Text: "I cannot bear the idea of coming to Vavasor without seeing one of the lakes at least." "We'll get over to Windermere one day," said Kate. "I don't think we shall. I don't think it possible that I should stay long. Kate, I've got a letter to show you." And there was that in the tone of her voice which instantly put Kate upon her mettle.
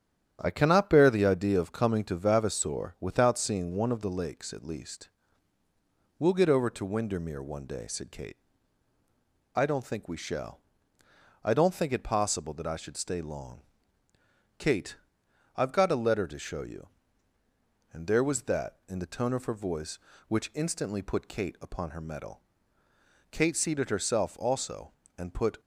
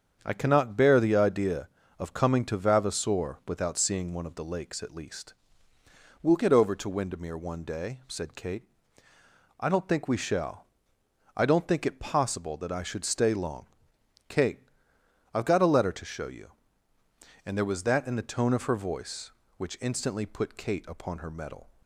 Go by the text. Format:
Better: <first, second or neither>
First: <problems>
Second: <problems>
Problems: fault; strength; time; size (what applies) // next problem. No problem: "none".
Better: second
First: starts louder than the rest; strong; until 1.4 s; 9.5 dB // goes on to say "Kate seated herself also and put"; strong; from 23.2 s on; 2.3 s long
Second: starts louder than the rest; strong; until 1.2 s; 7.5 dB